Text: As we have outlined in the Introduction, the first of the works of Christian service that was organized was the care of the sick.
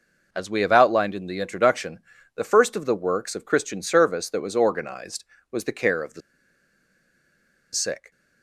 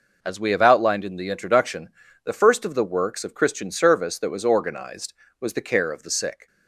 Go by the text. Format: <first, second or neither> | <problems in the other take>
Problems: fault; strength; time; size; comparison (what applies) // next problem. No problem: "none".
second | pauses between "the" and "sick"; strong; at 6.2 s; 1.5 s long